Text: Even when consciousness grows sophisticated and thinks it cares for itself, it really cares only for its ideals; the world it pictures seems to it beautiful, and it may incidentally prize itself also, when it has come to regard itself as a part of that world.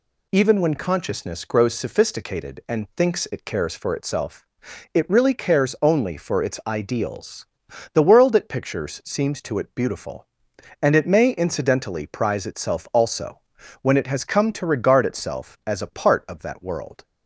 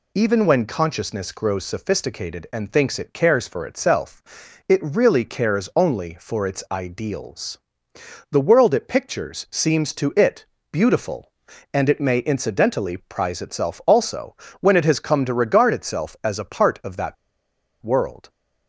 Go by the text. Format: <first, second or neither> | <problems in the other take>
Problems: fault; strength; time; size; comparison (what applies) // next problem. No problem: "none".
first | pauses between "it" and "beautiful"; slight; at 10.4 s; 0.28 s long // pauses between "that" and "world"; noticeable; at 17.1 s; 0.67 s long